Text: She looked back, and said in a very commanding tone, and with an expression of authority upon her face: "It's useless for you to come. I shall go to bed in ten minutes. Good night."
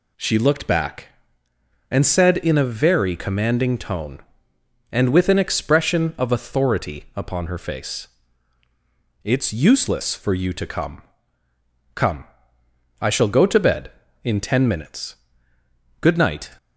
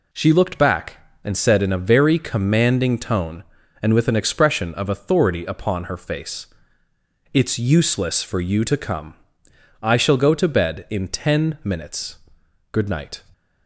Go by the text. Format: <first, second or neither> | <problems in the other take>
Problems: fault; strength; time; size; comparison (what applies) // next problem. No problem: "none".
second | says "come" twice; at 11.9 s